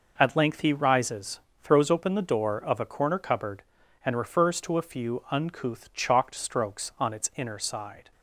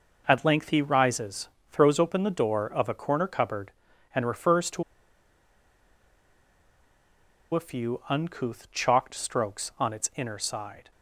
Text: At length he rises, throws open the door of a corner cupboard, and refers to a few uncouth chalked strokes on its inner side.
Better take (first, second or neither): first